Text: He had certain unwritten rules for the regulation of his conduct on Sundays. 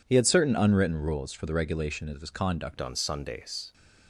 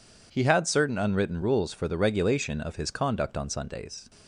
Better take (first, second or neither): second